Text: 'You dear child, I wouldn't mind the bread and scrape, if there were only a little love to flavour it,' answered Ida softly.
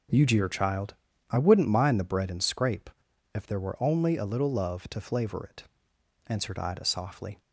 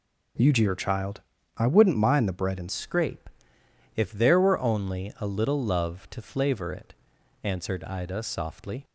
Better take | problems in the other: first | changes voice at "scrape"; from 2.7 s on; 6.1 s long

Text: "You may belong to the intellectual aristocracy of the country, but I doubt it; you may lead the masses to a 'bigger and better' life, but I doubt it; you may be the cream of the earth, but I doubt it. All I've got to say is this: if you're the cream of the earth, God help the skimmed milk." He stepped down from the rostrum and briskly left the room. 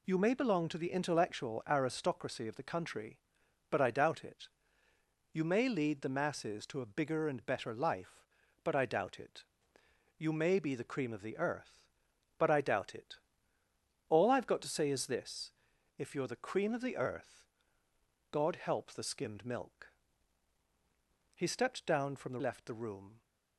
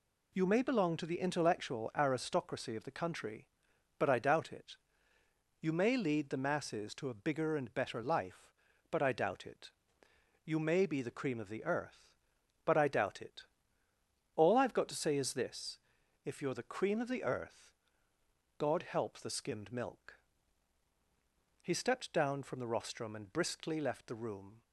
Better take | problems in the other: second | skips "rostrum and briskly"; at 22.3 s

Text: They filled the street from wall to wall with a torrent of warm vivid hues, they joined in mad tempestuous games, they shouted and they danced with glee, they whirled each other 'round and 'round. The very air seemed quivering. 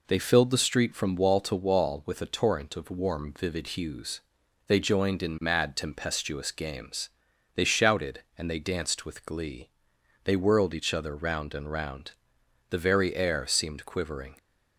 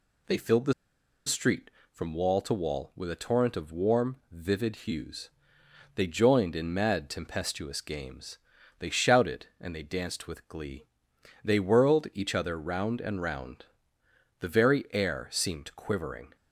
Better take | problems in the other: first | pauses between "the" and "street"; noticeable; at 0.7 s; 0.54 s long

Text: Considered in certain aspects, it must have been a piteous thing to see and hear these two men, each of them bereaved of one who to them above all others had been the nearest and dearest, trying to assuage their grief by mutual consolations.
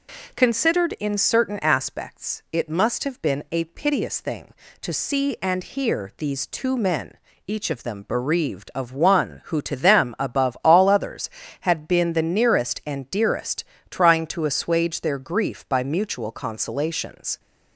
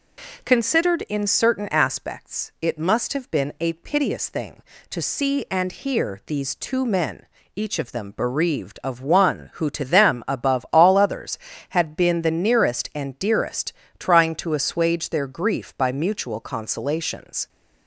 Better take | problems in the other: neither | none

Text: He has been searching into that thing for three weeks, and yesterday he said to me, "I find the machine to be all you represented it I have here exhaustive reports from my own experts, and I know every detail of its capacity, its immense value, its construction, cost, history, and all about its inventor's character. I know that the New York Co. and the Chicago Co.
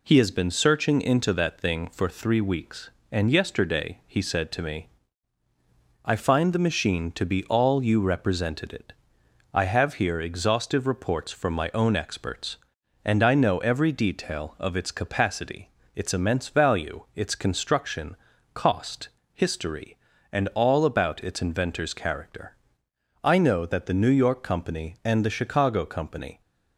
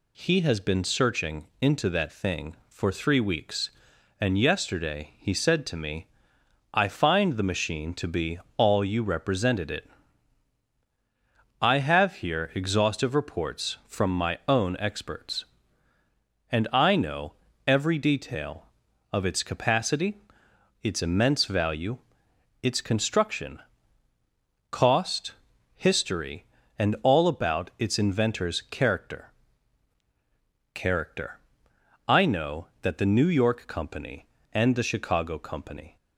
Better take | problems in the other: first | pauses between "be" and "all"; slight; at 8.3 s; 0.18 s long // pauses between "it" and "I"; strong; at 9.8 s; 1.7 s long; noticeable in the first // pauses between "know" and "every"; slight; at 17.3 s; 0.34 s long // says "character" twice; at 30.7 s

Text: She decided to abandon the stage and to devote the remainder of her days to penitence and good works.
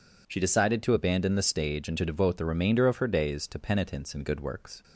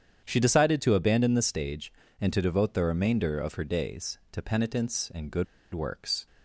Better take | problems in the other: first | starts louder than the rest; strong; until 1.2 s; 8.5 dB // pauses between "good" and "works"; slight; at 5.4 s; 0.28 s long

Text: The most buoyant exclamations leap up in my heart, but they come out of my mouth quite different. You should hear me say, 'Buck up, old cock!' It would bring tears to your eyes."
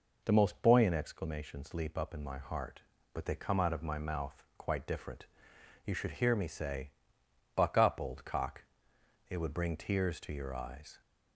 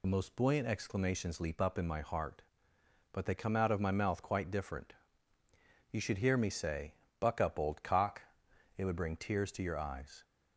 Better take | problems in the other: first | loses the start of "The"; at 0.0 s; 65 ms

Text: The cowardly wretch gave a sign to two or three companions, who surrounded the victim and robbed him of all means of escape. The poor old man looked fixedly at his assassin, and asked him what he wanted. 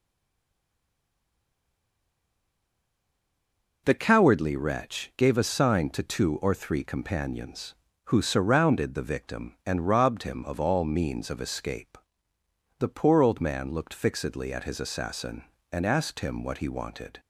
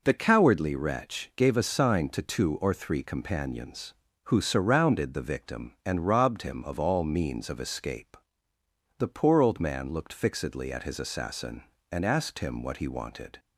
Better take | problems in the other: second | stays silent before the first word; strong; until 3.8 s; 3.8 s long

